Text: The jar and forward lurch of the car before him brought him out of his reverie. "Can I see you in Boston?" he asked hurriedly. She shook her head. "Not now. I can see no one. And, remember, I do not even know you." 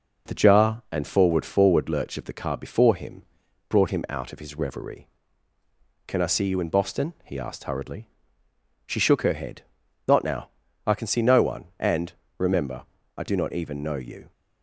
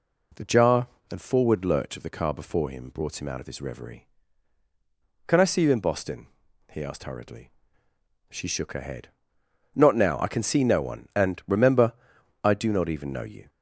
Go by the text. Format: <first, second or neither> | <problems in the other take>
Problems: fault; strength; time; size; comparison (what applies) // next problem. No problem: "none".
second | says "forward" twice; at 1.4 s // pauses between "him" and "brought"; noticeable; at 3.2 s; 0.46 s long